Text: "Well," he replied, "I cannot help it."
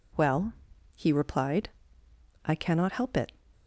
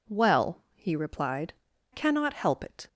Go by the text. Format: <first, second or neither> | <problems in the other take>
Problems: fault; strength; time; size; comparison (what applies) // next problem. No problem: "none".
first | skips "I"; at 1.7 s